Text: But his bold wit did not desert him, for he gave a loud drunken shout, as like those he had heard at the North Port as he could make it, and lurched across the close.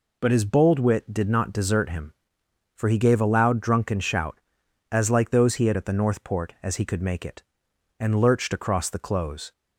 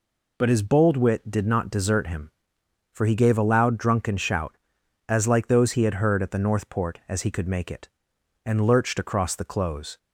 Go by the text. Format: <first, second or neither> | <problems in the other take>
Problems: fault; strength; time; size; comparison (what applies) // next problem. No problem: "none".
second | skips "heard"; at 5.7 s